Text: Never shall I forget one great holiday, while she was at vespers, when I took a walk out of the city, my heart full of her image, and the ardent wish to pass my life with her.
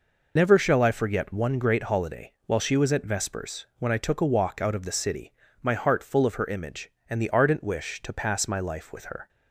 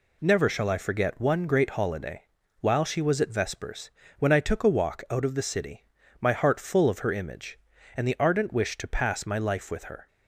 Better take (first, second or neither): second